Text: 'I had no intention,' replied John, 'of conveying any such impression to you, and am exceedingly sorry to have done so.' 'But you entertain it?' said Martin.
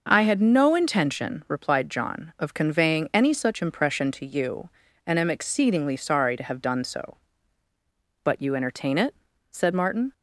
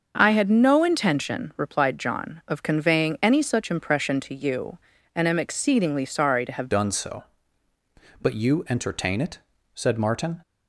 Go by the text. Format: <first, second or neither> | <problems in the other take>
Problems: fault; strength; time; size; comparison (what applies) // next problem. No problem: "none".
first | starts louder than the rest; until 1.1 s; 6.5 dB; noticeable in the first // changes voice at "done"; from 6.7 s on; 3.7 s long